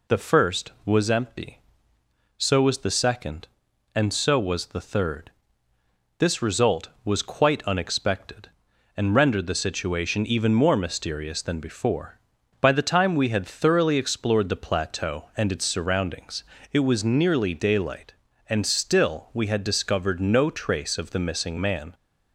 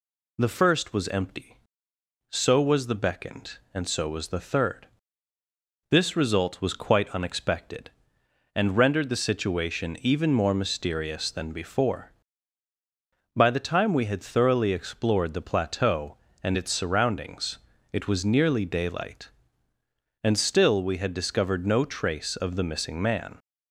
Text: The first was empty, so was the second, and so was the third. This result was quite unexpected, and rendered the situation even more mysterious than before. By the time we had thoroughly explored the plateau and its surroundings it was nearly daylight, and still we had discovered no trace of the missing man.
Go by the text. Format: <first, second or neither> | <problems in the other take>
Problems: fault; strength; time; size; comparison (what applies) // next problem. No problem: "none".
first | says "beckoned" for "second"; at 2.9 s // pauses between "surroundings" and "it"; slight; at 17.5 s; 0.34 s long; slight in the first